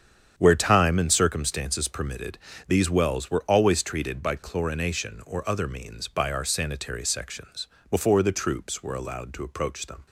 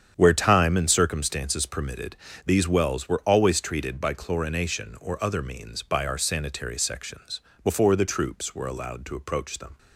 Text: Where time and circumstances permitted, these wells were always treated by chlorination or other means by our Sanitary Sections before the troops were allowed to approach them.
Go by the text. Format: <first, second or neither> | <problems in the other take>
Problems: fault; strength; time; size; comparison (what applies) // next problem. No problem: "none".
neither | starts louder than the rest; strong; the same in both // pauses between "Sections" and "before"; slight; the same in both